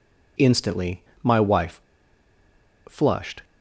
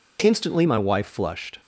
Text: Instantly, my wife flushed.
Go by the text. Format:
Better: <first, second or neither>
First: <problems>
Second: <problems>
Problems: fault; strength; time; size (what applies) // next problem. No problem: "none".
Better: second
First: pauses between "wife" and "flushed"; at 1.7 s; 1.0 s long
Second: none